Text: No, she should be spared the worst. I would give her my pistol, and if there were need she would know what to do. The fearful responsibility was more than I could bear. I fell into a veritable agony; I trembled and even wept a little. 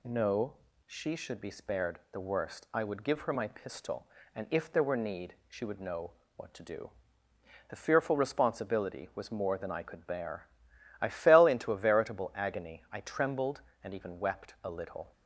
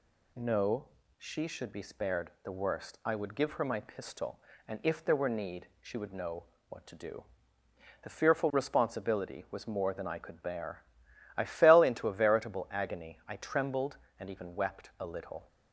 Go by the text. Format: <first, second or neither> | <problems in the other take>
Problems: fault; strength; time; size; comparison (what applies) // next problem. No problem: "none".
neither | pauses between "know" and "what"; slight; the same in both